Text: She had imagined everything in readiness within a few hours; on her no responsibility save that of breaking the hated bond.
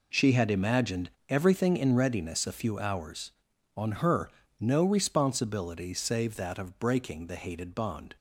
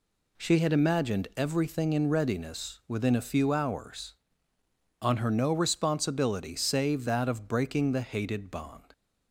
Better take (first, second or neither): second